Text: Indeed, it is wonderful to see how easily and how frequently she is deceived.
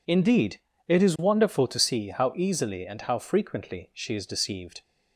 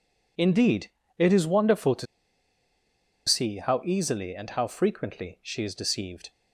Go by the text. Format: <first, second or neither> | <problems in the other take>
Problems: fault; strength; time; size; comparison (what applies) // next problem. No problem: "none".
first | pauses between "to" and "see"; at 2.0 s; 1.2 s long